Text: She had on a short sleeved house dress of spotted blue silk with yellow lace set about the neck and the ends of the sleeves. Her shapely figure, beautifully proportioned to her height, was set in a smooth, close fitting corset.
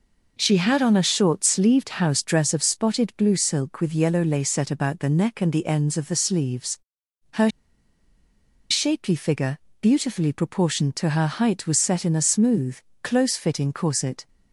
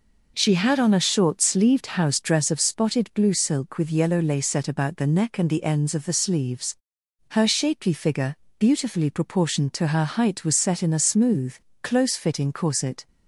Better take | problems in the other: second | pauses between "Her" and "shapely"; at 7.4 s; 1.2 s long

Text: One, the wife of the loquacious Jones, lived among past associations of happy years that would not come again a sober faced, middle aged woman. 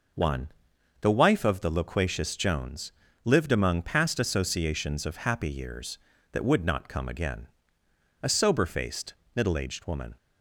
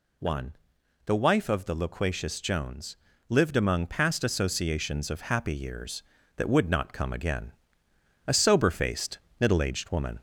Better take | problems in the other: first | gets louder; slight; throughout; 2.5 dB // pauses between "again" and "a"; noticeable; at 7.5 s; 0.74 s long; noticeable in the first

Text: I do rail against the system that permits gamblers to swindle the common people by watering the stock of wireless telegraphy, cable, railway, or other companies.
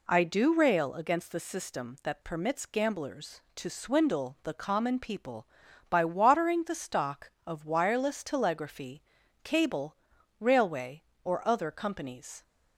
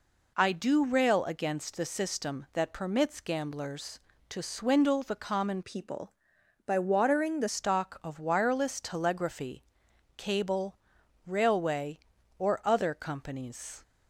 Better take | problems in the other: first | changes voice from "people" to "the"; from 5.6 to 7.4 s; 1.8 s long

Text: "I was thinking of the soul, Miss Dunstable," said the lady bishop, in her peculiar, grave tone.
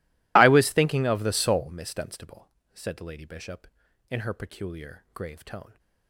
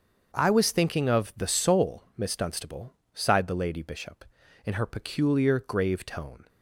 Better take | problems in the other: first | starts louder than the rest; until 1.3 s; 6.5 dB // says "sighed" for "said"; at 3.1 s

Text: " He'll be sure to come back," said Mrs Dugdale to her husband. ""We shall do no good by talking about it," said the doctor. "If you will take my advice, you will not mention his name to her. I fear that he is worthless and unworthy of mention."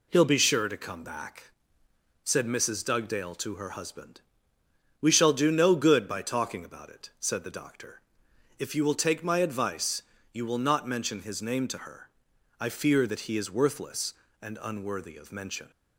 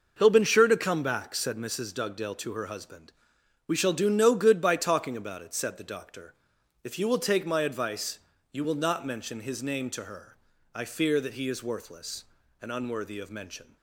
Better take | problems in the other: first | says "been" for "be"; at 0.3 s

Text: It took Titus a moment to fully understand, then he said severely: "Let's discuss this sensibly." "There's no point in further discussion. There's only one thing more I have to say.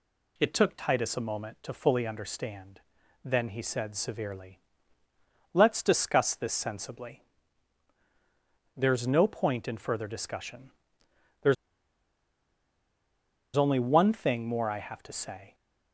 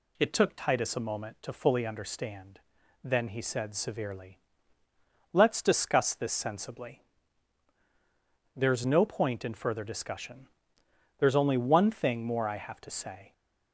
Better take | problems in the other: second | pauses between "There's" and "only"; strong; at 11.5 s; 2.0 s long

